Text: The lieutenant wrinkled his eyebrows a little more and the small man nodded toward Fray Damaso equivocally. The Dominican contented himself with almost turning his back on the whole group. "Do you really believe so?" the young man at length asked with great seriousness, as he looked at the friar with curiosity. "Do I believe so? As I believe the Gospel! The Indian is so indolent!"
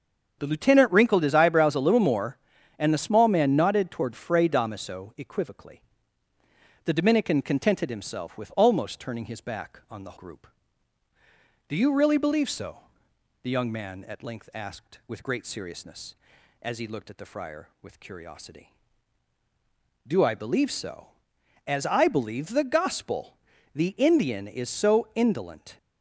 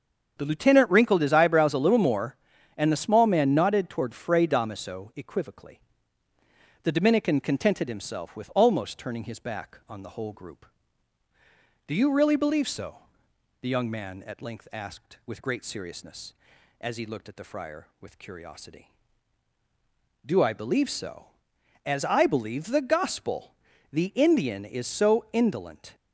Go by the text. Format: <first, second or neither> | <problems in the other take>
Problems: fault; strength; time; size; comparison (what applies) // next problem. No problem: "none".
second | starts louder than the rest; strong; until 1.4 s; 7.5 dB; strong in the second // skips "whole"; at 10.1 s